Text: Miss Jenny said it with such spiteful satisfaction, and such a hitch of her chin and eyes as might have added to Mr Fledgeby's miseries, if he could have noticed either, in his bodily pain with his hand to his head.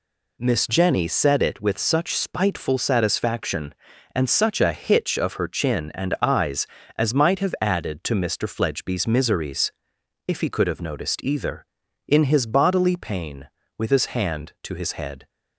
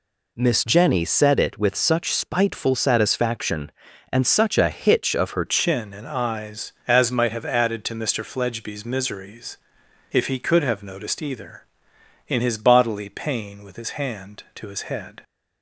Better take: first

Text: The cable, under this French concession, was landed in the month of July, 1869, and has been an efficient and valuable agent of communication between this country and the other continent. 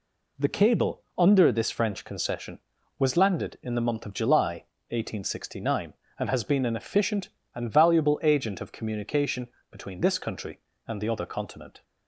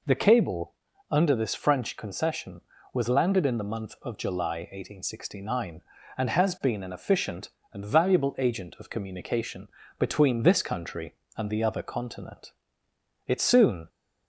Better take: first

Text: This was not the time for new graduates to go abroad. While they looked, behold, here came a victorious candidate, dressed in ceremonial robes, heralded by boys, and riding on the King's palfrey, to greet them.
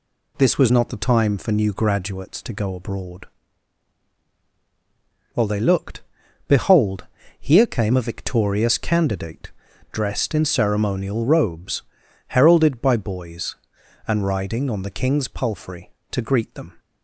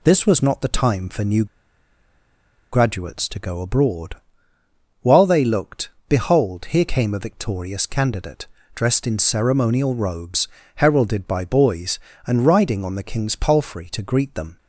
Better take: first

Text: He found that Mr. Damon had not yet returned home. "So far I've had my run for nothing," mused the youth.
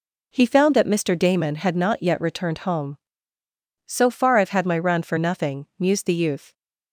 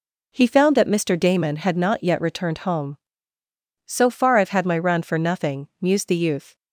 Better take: neither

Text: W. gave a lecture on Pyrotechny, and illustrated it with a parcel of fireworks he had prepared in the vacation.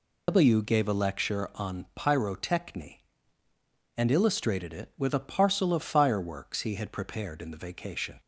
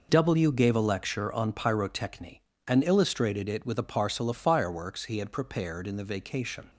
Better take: second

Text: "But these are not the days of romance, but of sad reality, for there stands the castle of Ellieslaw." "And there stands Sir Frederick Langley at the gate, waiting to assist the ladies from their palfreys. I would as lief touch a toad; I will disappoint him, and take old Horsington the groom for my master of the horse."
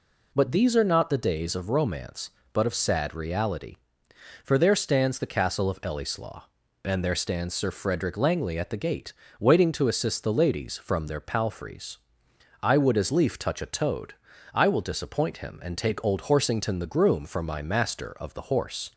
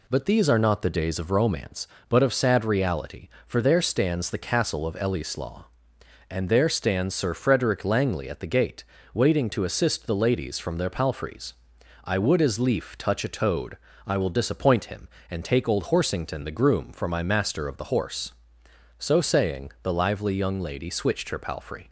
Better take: first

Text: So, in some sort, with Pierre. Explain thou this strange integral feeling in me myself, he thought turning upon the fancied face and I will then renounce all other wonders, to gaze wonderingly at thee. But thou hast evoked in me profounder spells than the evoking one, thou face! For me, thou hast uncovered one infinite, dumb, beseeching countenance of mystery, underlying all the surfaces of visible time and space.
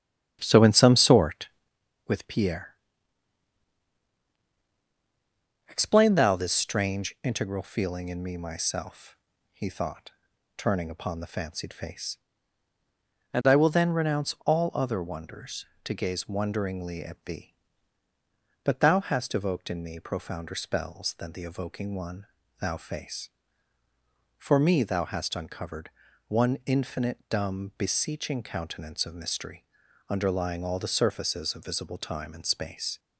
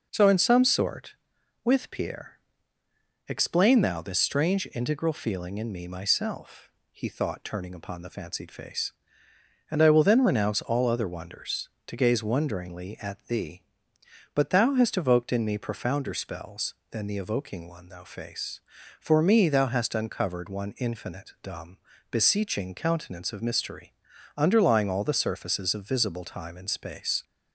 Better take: second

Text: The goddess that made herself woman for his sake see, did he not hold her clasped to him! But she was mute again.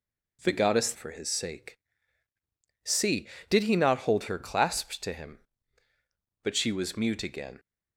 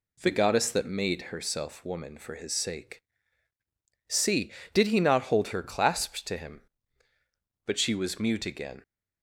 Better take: second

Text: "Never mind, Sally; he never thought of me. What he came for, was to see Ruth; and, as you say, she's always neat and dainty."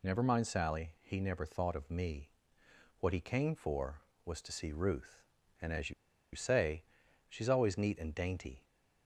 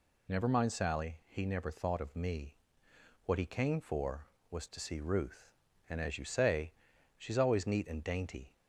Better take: second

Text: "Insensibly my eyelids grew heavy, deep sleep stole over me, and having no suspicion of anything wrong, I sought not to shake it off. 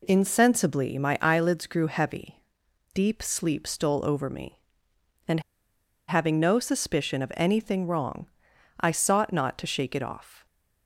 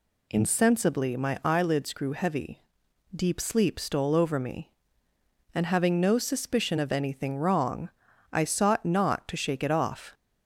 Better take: second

